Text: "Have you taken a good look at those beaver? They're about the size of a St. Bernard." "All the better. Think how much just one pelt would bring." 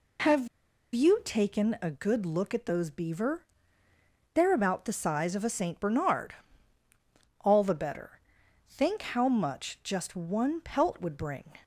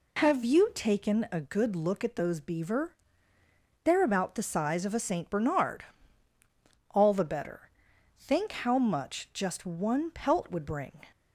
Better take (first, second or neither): second